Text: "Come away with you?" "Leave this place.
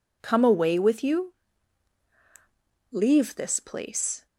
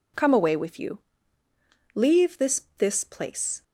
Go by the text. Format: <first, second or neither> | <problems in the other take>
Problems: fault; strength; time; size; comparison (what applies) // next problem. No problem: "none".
first | says "this" twice; at 2.7 s